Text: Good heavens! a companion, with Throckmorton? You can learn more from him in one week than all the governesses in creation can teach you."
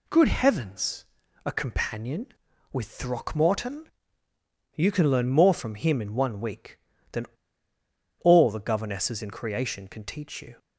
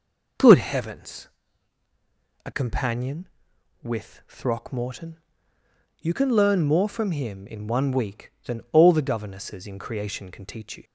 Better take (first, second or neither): second